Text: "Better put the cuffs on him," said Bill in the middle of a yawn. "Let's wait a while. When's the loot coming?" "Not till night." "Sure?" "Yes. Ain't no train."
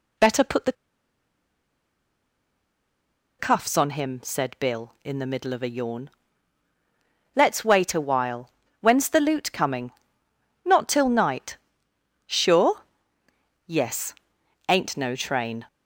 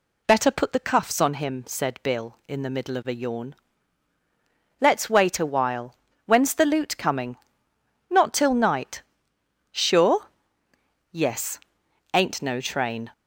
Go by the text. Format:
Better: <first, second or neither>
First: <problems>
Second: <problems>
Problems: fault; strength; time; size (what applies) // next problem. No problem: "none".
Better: second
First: pauses between "the" and "cuffs"; strong; at 0.7 s; 2.6 s long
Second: none